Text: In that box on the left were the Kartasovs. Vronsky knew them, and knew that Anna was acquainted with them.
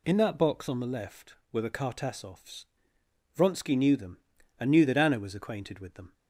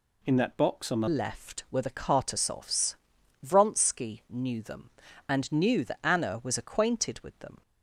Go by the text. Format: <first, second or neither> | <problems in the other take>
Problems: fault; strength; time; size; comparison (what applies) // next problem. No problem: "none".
first | changes voice at "left"; from 1.0 s on; 6.6 s long